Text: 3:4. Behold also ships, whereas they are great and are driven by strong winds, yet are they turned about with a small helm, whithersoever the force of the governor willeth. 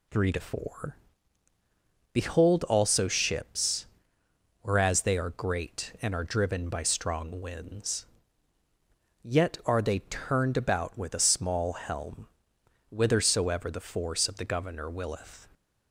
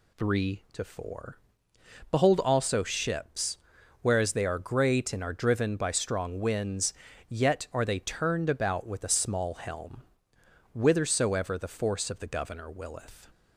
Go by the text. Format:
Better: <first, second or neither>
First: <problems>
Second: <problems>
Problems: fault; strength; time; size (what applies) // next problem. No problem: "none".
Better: neither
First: none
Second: none